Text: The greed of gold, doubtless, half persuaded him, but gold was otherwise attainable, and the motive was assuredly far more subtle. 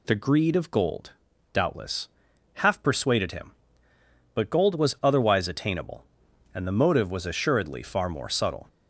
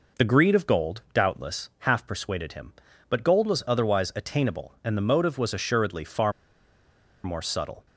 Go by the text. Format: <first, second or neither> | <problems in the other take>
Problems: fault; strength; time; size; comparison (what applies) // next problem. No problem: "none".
first | pauses between "far" and "more"; noticeable; at 6.3 s; 0.92 s long